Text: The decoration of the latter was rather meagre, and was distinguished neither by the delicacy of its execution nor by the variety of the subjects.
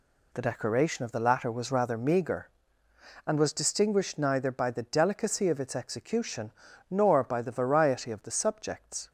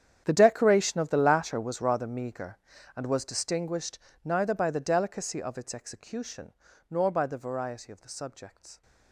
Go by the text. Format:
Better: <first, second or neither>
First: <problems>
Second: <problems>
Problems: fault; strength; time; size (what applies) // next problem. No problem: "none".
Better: first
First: pauses between "execution" and "nor"; at 6.5 s; 0.38 s long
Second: gets quieter; strong; throughout; 17.5 dB // pauses between "distinguished" and "neither"; slight; at 3.9 s; 0.24 s long // pauses between "execution" and "nor"; at 6.5 s; 0.38 s long